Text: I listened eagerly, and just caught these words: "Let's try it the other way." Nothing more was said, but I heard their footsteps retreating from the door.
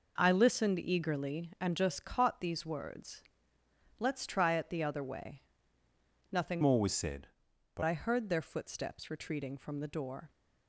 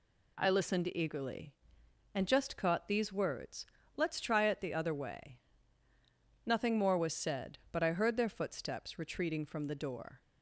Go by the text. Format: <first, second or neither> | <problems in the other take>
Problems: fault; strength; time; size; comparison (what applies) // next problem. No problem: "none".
second | changes voice from "more" to "but"; from 6.6 to 7.8 s; 1.2 s long